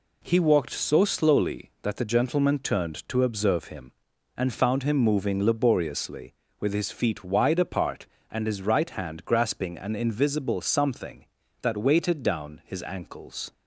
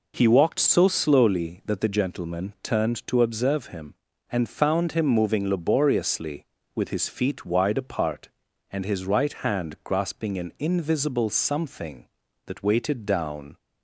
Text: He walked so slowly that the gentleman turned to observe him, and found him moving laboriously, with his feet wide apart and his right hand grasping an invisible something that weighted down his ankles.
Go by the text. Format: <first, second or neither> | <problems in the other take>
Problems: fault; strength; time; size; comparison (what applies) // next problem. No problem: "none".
first | stops before "his ankles"; at 13.5 s